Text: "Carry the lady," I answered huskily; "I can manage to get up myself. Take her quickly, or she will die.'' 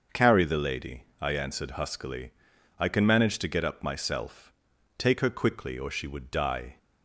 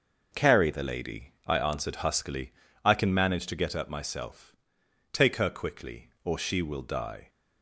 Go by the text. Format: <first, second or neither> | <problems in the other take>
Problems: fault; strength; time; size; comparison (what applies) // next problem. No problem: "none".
second | starts louder than the rest; until 1.3 s; 6.5 dB // says "would" for "will"; at 6.0 s